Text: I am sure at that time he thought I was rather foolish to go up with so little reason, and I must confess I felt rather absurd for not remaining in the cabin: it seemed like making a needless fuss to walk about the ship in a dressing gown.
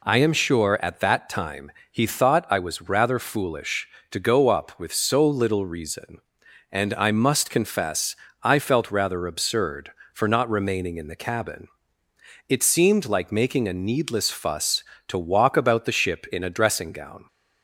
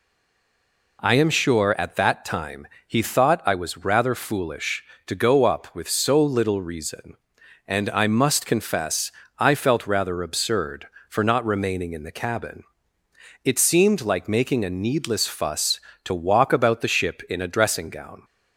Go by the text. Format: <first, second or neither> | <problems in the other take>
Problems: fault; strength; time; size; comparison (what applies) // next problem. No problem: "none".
first | stays silent before the first word; until 0.9 s; 0.9 s long // pauses between "time" and "he"; slight; at 2.6 s; 0.18 s long; slight in the first // pauses between "confess" and "I"; slight; at 9.0 s; 0.30 s long; slight in the first